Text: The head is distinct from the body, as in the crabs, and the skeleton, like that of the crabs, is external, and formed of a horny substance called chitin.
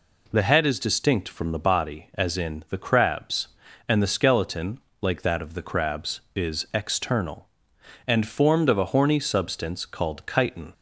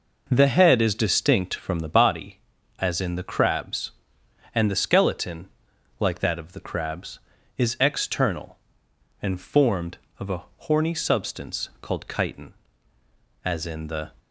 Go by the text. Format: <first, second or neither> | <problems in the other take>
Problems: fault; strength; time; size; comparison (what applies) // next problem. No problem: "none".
first | pauses between "a" and "horny"; slight; at 10.4 s; 0.16 s long // goes on to say "As in the"; noticeable; from 13.4 s on; 0.66 s long